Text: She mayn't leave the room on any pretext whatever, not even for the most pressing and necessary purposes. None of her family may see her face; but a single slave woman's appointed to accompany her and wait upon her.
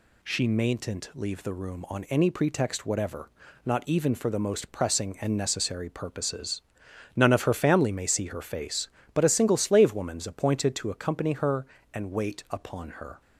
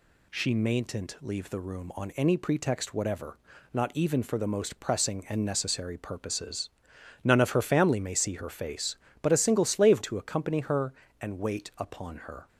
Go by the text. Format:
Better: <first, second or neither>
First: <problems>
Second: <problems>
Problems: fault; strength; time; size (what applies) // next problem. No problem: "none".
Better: first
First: none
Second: skips "woman's appointed"; at 10.0 s